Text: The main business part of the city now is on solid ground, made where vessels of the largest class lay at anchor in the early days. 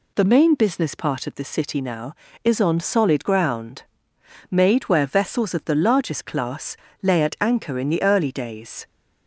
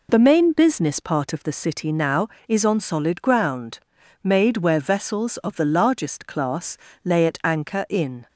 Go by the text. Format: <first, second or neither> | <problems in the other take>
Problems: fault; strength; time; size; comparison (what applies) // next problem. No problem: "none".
first | pauses between "class" and "lay"; slight; at 6.7 s; 0.26 s long; slight in the first // stops before "the early days"; at 8.2 s